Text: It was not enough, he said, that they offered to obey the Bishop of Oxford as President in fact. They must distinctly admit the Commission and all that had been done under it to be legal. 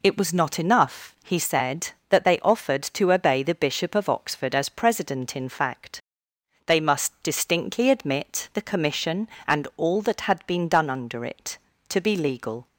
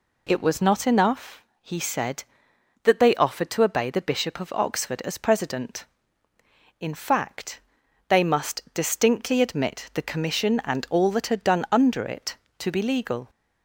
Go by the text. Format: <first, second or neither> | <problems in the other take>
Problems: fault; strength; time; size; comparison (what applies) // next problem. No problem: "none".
first | skips "been"; at 11.4 s